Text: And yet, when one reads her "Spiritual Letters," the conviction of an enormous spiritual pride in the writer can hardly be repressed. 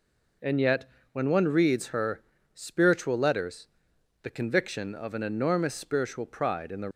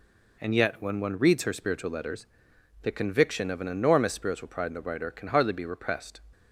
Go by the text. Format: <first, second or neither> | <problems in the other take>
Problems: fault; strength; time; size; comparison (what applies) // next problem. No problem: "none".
second | pauses between "her" and "Spiritual"; slight; at 2.2 s; 0.32 s long // stops before "writer can hardly be repressed"; at 6.9 s